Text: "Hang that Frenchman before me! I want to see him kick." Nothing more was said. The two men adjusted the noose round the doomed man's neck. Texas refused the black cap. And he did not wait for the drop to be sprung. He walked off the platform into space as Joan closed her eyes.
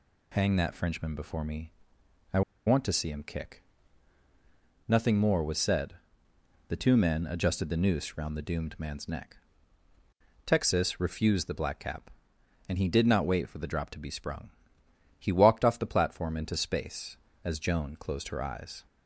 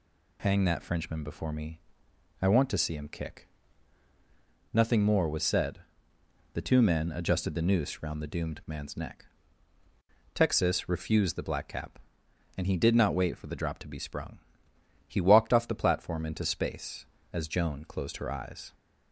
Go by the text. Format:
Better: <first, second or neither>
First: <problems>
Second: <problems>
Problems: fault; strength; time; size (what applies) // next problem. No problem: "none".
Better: second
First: pauses between "I" and "want"; slight; at 2.4 s; 0.26 s long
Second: none